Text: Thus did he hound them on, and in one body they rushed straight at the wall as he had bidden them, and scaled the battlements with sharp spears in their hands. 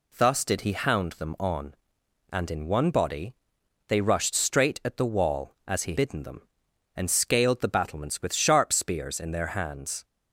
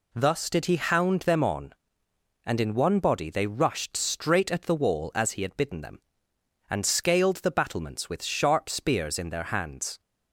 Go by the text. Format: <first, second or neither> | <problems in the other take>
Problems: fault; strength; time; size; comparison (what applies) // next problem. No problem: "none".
second | pauses between "body" and "they"; noticeable; at 3.3 s; 0.54 s long // skips "had"; at 5.9 s